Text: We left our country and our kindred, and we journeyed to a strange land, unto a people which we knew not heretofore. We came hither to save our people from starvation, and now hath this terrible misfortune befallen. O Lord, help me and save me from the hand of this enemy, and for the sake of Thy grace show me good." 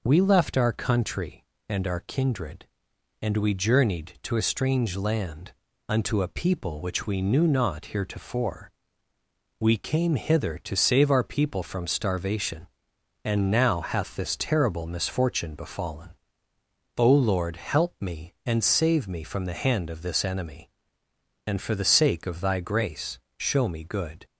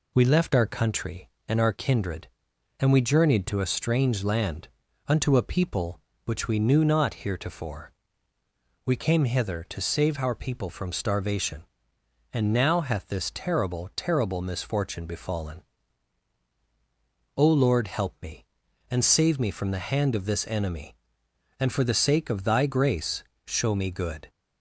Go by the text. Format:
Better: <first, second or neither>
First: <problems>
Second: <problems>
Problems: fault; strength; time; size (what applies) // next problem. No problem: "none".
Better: first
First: pauses between "grace" and "show"; slight; at 23.1 s; 0.18 s long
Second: says "terrible" twice; at 13.9 s // pauses between "grace" and "show"; slight; at 23.2 s; 0.22 s long